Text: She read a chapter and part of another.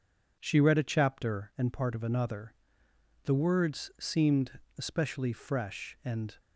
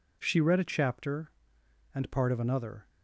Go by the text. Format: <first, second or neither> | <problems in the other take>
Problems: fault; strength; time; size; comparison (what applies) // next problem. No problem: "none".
second | goes on to say "The words seemed especially fresh and"; strong; from 3.2 s on; 3.1 s long